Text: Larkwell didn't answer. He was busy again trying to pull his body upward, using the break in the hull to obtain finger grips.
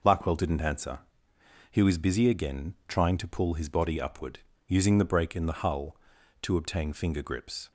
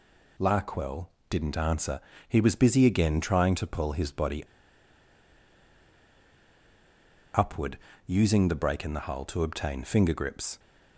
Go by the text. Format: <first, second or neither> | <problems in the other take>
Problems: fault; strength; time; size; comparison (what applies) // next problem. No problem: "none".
first | pauses between "Larkwell" and "didn't"; slight; at 1.0 s; 0.20 s long // pauses between "body" and "upward"; strong; at 4.4 s; 2.9 s long